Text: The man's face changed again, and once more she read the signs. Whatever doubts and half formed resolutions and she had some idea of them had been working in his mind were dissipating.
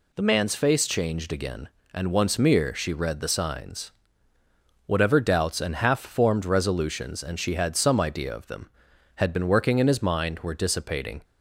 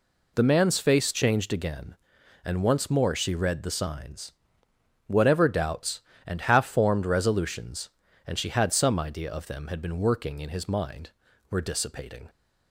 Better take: second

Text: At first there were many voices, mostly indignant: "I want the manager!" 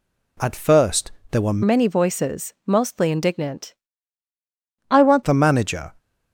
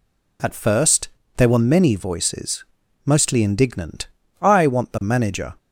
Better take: second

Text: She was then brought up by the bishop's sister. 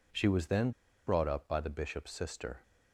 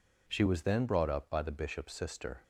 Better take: second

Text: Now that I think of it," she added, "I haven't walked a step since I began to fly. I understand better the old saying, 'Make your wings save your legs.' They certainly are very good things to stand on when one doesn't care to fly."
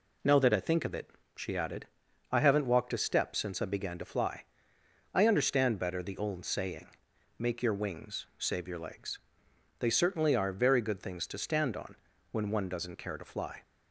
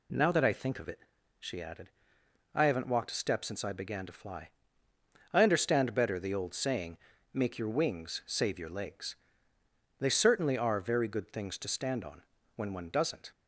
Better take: first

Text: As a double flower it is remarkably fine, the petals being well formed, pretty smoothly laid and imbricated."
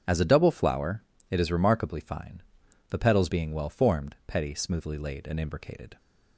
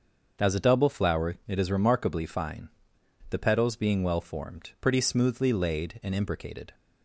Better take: second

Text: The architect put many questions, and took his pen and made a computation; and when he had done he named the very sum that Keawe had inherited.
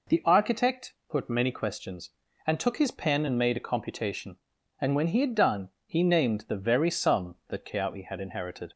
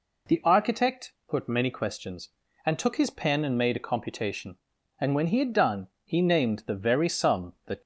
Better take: first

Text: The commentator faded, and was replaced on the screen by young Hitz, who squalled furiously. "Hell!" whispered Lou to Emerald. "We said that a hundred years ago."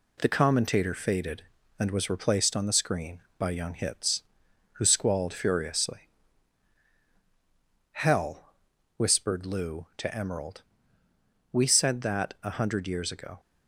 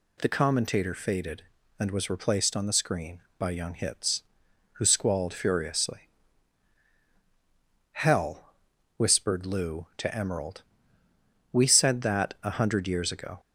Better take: second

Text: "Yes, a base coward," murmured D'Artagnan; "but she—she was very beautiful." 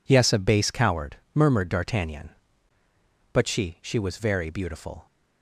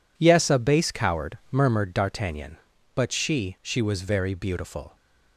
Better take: neither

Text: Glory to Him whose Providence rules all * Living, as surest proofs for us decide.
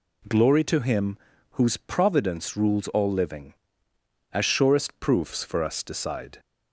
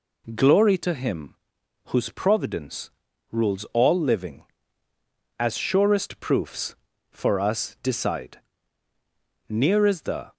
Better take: first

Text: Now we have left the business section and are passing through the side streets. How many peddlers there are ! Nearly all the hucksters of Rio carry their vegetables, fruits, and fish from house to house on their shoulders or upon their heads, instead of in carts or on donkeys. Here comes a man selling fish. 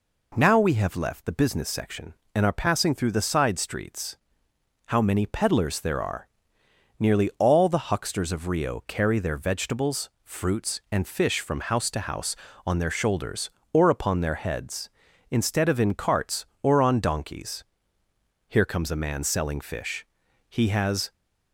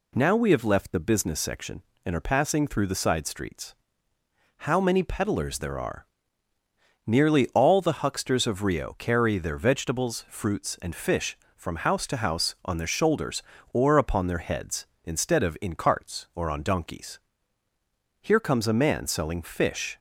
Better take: second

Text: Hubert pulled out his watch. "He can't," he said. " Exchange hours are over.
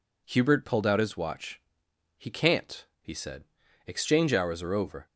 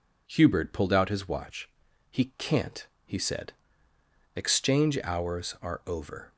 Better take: neither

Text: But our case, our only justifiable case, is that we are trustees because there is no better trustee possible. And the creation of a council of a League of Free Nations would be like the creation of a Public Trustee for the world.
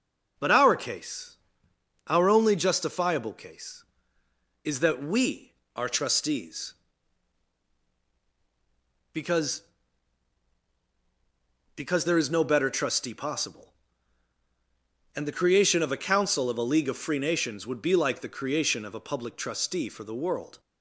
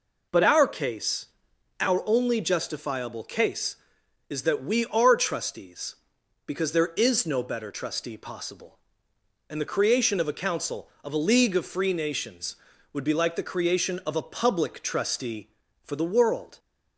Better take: second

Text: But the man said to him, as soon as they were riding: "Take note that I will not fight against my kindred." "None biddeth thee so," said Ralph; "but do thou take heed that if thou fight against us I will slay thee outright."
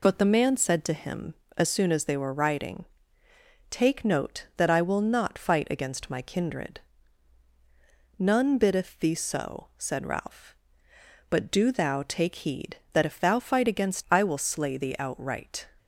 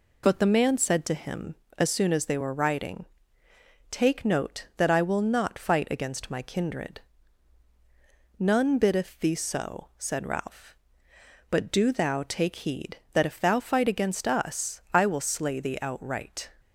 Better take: second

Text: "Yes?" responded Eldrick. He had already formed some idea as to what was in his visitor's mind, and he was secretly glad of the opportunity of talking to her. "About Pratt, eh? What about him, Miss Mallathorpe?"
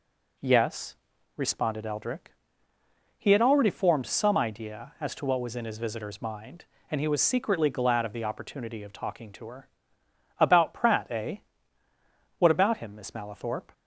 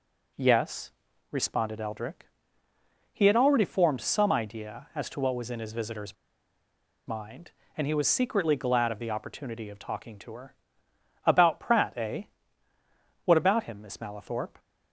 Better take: first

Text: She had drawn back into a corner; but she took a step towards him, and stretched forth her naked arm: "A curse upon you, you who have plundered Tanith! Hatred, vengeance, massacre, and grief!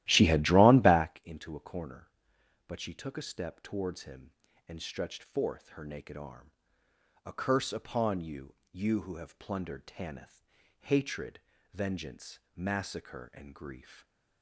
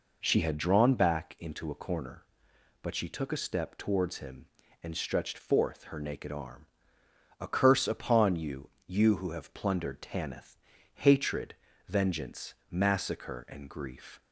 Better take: second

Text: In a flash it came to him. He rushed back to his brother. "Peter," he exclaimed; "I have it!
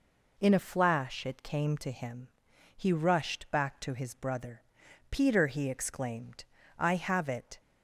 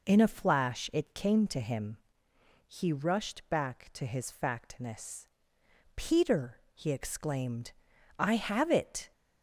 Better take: first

